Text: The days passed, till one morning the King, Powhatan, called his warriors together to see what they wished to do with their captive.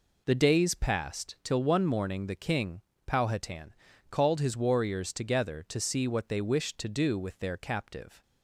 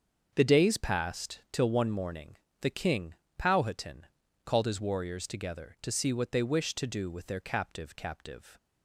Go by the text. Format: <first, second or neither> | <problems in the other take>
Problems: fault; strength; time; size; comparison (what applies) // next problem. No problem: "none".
first | starts louder than the rest; until 1.3 s; 7 dB // pauses between "morning" and "the"; slight; at 2.3 s; 0.24 s long // says "captive" twice; at 7.9 s